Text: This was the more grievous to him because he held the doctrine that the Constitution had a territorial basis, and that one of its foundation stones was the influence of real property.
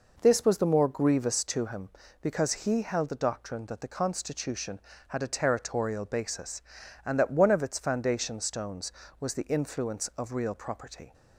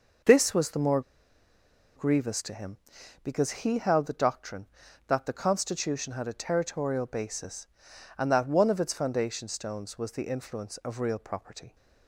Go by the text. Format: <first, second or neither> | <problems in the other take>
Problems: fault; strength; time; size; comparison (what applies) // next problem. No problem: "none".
first | pauses between "more" and "grievous"; noticeable; at 1.0 s; 0.95 s long